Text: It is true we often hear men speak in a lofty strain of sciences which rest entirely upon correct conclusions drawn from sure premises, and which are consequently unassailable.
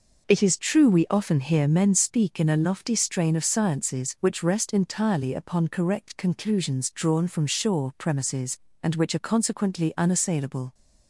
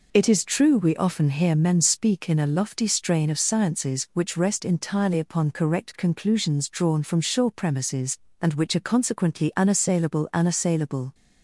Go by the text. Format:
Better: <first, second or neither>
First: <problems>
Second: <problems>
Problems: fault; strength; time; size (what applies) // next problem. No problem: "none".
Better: first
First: none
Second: says "unassailable" twice; at 10.3 s